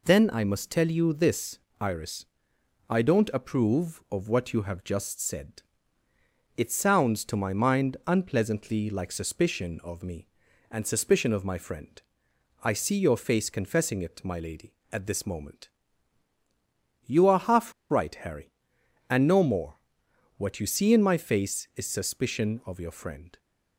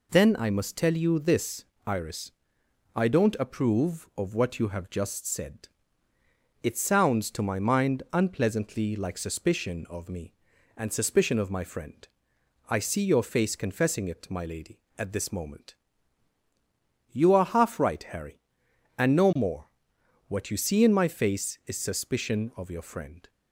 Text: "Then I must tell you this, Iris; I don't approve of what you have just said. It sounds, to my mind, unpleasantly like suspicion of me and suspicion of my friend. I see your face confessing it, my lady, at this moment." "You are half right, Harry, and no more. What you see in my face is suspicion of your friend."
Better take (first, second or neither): second